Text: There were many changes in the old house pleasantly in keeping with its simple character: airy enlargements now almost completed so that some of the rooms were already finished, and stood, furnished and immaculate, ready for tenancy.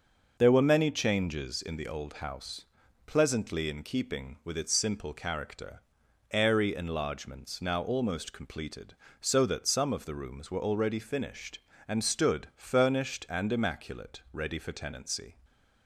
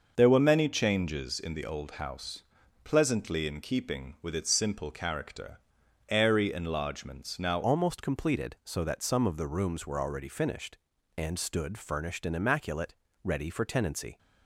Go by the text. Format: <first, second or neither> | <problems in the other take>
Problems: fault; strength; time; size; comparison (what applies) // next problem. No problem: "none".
first | starts louder than the rest; noticeable; until 1.1 s; 6 dB; noticeable in the first // pauses between "house" and "pleasantly"; at 2.4 s; 0.40 s long; also in the first // changes voice at "almost"; from 7.6 s on; 6.5 s long